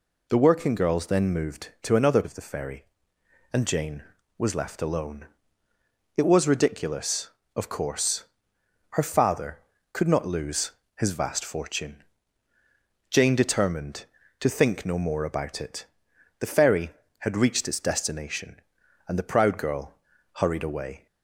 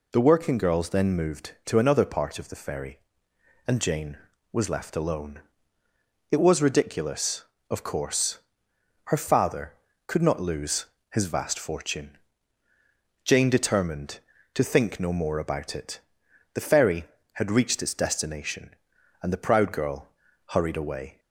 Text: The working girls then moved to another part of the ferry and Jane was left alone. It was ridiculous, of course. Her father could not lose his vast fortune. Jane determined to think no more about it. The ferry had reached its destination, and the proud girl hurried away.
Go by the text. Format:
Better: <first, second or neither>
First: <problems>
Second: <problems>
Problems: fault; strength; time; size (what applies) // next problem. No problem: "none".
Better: second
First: skips "part"; at 2.2 s // pauses between "lose" and "his"; slight; at 10.7 s; 0.26 s long // pauses between "girl" and "hurried"; at 19.9 s; 0.38 s long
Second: pauses between "lose" and "his"; slight; at 10.8 s; 0.26 s long // pauses between "girl" and "hurried"; at 20.0 s; 0.37 s long